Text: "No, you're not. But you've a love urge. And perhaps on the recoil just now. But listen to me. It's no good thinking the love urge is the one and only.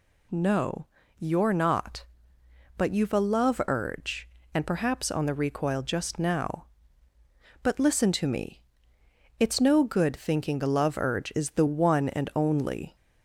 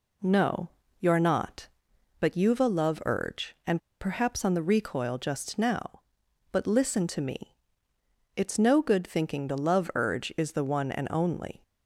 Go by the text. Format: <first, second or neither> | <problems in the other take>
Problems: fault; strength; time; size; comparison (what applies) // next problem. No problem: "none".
first | pauses between "And" and "perhaps"; slight; at 3.7 s; 0.21 s long